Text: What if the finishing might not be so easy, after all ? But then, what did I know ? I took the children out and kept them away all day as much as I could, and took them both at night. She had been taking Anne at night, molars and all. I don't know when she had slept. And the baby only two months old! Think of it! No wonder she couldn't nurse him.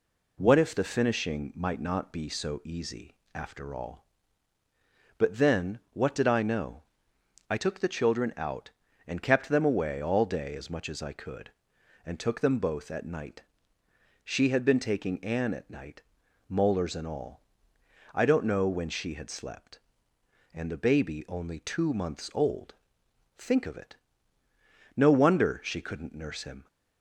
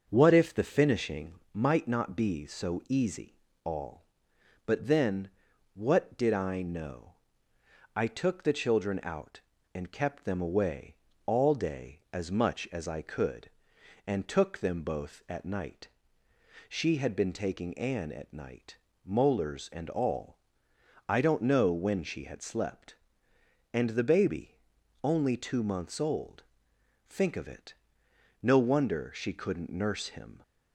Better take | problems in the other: first | starts louder than the rest; until 1.1 s; 6.5 dB // pauses between "finishing" and "might"; slight; at 1.3 s; 0.18 s long // skips "after"; at 3.5 s // pauses between "away" and "all"; slight; at 10.9 s; 0.30 s long // pauses between "baby" and "only"; noticeable; at 24.5 s; 0.46 s long

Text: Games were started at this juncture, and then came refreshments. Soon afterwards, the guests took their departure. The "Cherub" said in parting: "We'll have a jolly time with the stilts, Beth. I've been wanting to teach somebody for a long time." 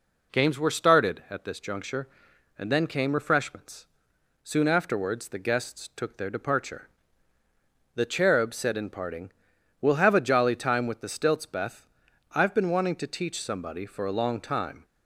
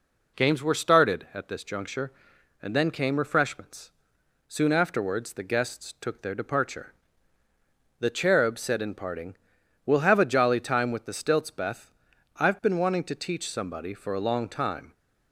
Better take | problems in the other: neither | none

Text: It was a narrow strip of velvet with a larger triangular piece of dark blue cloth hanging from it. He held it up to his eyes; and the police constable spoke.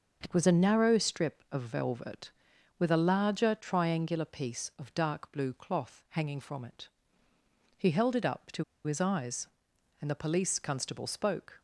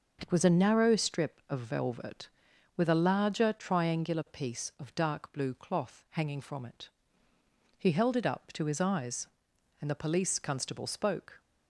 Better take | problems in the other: second | starts louder than the rest; noticeable; until 1.2 s; 6 dB; noticeable in the second // pauses between "to" and "his"; slight; at 8.6 s; 0.22 s long

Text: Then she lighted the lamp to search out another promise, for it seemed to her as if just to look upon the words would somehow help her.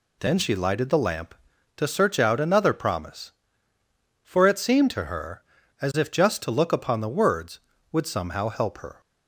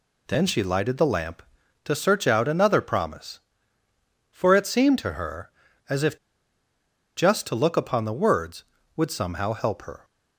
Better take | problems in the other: first | pauses between "if" and "just"; at 6.1 s; 1.0 s long

